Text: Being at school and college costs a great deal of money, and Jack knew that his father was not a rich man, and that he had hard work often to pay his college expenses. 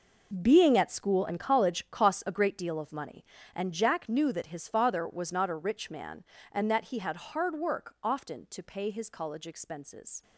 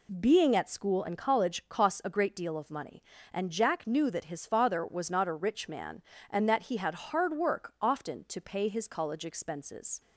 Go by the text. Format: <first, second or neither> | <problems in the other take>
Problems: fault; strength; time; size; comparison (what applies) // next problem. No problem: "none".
second | gets quieter; strong; throughout; 13 dB